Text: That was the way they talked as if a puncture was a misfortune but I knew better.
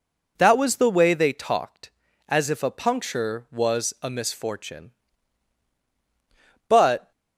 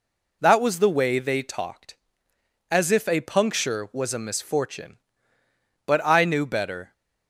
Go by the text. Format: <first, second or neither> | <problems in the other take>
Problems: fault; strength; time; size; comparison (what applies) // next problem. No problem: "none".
second | stops before "I knew better"; at 7.1 s